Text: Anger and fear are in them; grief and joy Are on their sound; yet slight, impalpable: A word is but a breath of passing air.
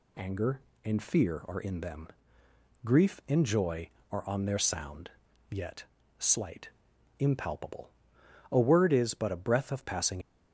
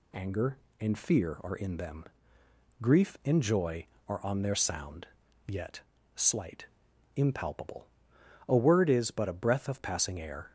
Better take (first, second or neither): second